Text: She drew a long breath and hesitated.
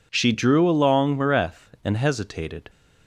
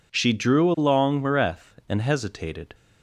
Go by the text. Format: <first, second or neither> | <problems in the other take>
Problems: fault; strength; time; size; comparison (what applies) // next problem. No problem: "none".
neither | none